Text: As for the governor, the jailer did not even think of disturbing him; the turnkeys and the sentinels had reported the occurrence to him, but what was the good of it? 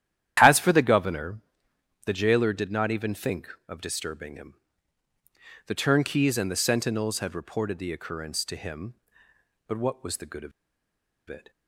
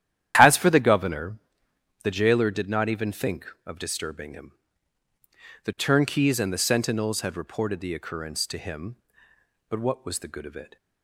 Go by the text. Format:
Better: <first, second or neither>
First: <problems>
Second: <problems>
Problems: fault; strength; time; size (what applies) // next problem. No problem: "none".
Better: second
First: starts louder than the rest; strong; until 1.4 s; 11 dB // pauses between "of" and "it"; noticeable; at 10.5 s; 0.78 s long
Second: starts louder than the rest; strong; until 1.3 s; 11 dB